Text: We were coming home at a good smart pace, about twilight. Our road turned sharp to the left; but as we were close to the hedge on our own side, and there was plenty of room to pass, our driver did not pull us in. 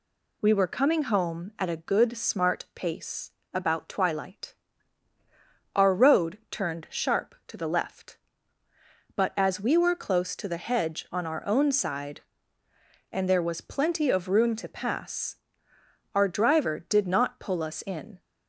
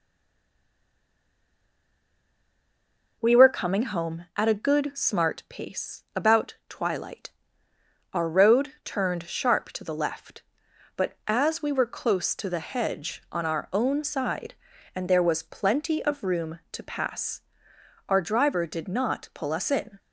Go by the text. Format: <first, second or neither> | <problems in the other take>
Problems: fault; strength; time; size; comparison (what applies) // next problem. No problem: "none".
first | stays silent before the first word; strong; until 3.2 s; 3.2 s long